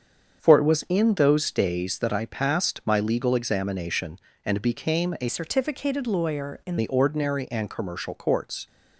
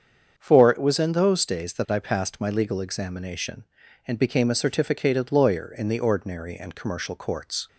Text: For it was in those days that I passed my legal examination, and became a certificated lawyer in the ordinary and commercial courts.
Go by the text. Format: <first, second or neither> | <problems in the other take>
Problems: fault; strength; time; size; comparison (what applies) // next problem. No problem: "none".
second | starts louder than the rest; strong; until 1.4 s; 7 dB; strong in the second // changes voice from "certificated" to "in"; from 5.2 to 6.7 s; 1.5 s long